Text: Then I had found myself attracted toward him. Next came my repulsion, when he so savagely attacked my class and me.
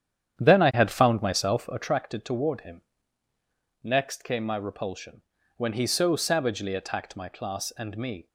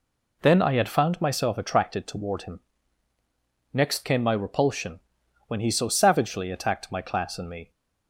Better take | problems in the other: second | starts louder than the rest; strong; until 2.0 s; 9.5 dB

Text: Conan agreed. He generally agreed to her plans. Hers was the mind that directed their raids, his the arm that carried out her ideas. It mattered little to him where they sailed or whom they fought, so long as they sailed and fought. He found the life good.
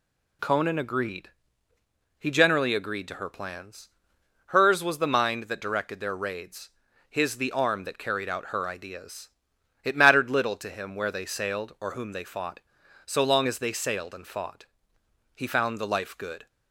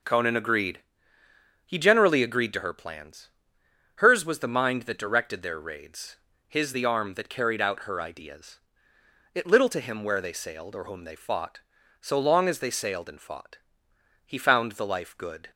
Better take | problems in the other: first | skips "mattered"; at 9.4 s

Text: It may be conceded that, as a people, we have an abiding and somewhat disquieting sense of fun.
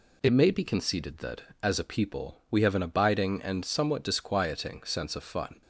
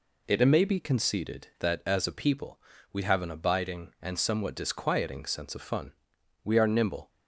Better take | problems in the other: first | goes on to say "We are nimble"; noticeable; from 6.4 s on; 0.66 s long

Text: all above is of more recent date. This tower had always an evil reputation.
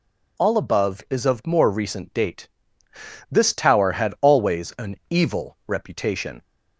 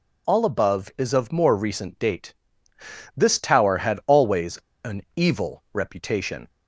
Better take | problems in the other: first | pauses between "always" and "an"; slight; at 4.5 s; 0.28 s long

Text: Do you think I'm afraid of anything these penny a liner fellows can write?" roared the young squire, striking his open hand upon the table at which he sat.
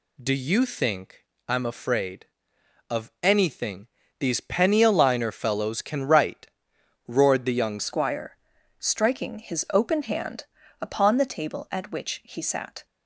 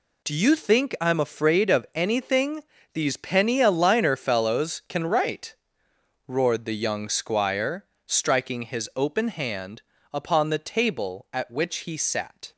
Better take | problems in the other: second | pauses between "think" and "I'm"; slight; at 1.2 s; 0.24 s long // pauses between "anything" and "these"; slight; at 3.8 s; 0.32 s long; slight in the second // changes voice at "squire"; from 7.7 s on; 5.1 s long // pauses between "hand" and "upon"; slight; at 10.4 s; 0.36 s long; slight in the second

